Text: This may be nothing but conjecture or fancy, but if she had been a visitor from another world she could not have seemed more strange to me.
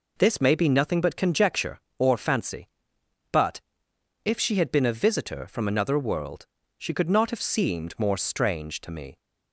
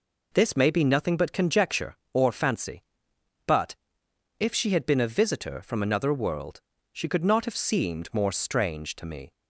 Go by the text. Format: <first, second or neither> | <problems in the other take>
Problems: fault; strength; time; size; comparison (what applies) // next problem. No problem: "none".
neither | pauses between "but" and "if"; noticeable; the same in both // pauses between "world" and "she"; slight; the same in both